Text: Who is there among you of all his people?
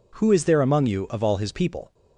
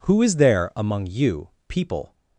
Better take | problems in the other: first | skips "of all his"; at 1.5 s

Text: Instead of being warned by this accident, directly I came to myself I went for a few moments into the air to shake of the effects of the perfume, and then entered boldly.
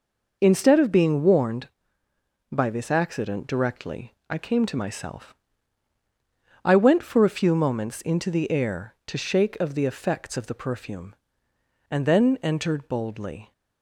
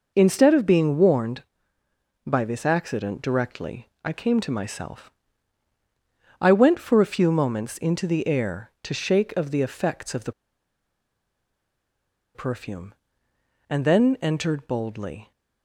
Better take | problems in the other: first | pauses between "directly" and "I"; slight; at 3.8 s; 0.16 s long; slight in the first // pauses between "myself" and "I"; strong; at 5.1 s; 1.3 s long; strong in the first // pauses between "the" and "perfume"; strong; at 10.3 s; 2.0 s long

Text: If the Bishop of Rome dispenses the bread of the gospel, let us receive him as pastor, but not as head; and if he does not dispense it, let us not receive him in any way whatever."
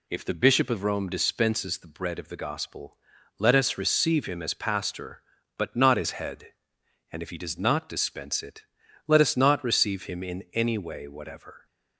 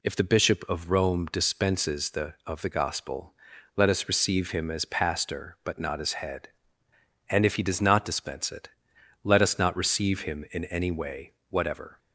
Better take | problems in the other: first | skips "bread"; at 2.4 s // pauses between "way" and "whatever"; slight; at 11.3 s; 0.18 s long

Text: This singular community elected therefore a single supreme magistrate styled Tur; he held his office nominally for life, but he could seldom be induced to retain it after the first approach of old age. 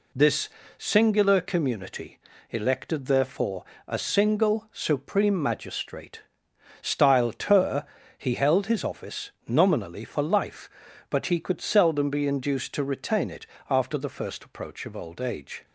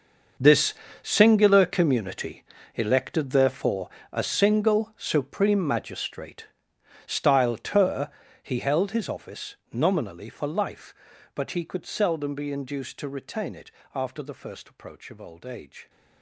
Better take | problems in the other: first | gets quieter; strong; throughout; 14.5 dB // pauses between "This" and "singular"; slight; at 0.7 s; 0.26 s long; slight in the first // pauses between "community" and "elected"; slight; at 2.4 s; 0.32 s long; slight in the first // pauses between "therefore" and "a"; slight; at 3.8 s; 0.24 s long; slight in the first // pauses between "magistrate" and "styled"; noticeable; at 6.4 s; 0.62 s long; noticeable in the first // pauses between "office" and "nominally"; slight; at 9.5 s; 0.16 s long; slight in the first // pauses between "it" and "after"; slight; at 13.7 s; 0.24 s long; slight in the first

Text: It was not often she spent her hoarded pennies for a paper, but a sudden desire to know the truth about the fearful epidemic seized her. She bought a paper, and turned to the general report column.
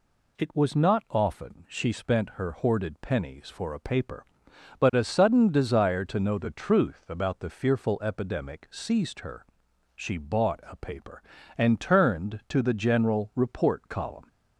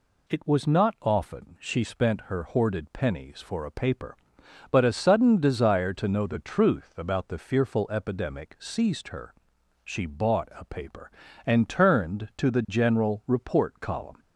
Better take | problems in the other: neither | none

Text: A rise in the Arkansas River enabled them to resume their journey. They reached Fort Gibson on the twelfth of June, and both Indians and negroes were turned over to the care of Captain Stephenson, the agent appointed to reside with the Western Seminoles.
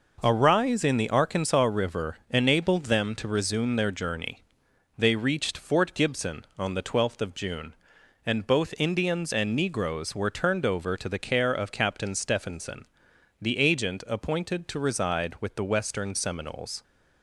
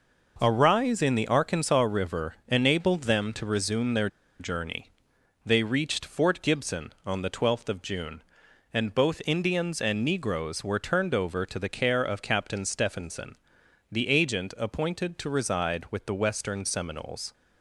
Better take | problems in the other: first | pauses between "their" and "journey"; slight; at 4.0 s; 0.32 s long

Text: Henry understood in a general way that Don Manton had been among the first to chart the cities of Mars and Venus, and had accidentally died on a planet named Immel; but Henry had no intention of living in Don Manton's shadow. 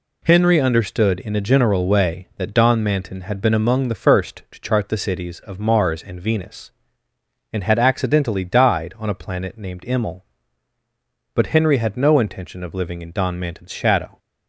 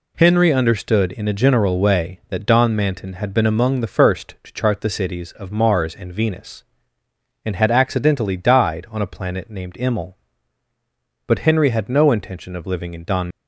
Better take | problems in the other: first | stops before "Manton's shadow"; at 13.3 s

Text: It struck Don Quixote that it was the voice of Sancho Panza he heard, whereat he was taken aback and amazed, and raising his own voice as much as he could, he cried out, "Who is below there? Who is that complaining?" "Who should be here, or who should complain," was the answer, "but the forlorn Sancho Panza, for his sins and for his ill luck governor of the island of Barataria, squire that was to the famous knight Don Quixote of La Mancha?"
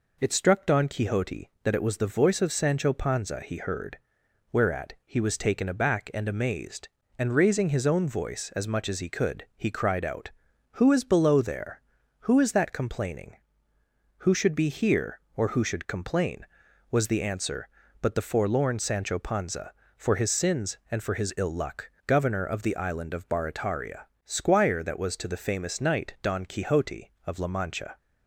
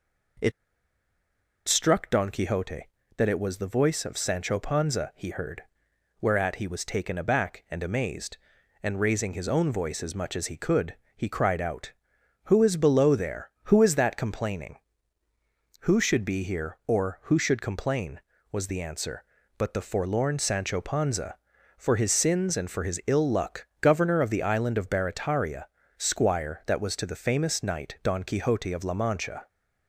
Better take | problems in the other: first | pauses between "It" and "struck"; at 0.5 s; 1.1 s long // pauses between "luck" and "governor"; slight; at 23.6 s; 0.16 s long; slight in the first

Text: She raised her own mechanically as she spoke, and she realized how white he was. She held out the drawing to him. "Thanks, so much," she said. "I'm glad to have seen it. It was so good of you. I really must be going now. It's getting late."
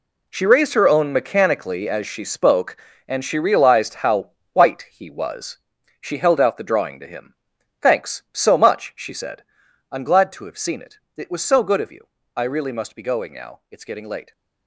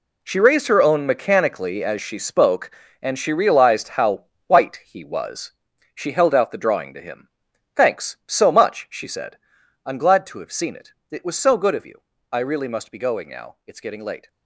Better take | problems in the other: neither | pauses between "how" and "white"; slight; the same in both

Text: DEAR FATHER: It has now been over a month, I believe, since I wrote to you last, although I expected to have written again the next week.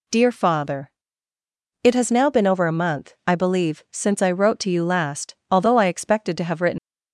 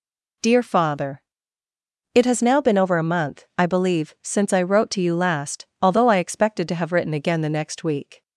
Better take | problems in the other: second | stops before "again the next week"; at 6.7 s

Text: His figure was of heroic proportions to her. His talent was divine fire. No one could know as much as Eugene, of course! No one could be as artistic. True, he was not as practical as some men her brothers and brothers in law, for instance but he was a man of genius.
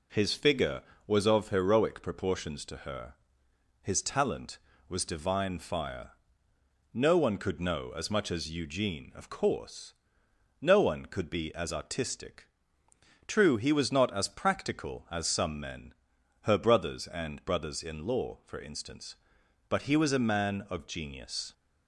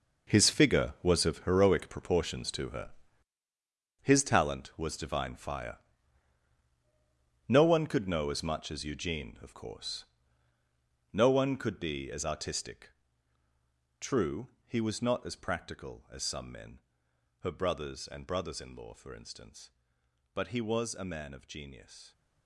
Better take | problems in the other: first | gets quieter; strong; throughout; 12.5 dB // pauses between "men" and "her"; noticeable; at 16.8 s; 0.62 s long; noticeable in the first

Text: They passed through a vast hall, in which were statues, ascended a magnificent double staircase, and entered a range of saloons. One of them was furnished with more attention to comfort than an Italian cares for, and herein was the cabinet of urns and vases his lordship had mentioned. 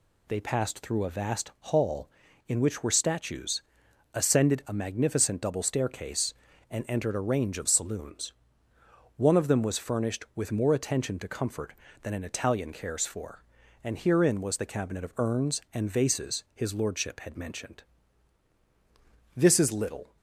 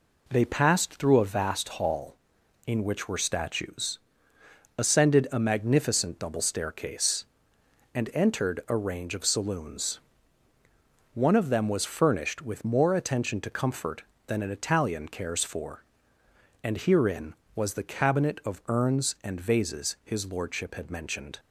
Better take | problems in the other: second | goes on to say "This is little"; noticeable; from 19.3 s on; 0.80 s long

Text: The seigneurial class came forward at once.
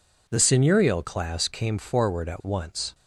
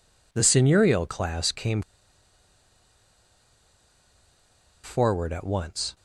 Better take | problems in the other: first | pauses between "came" and "forward"; strong; at 1.8 s; 3.0 s long

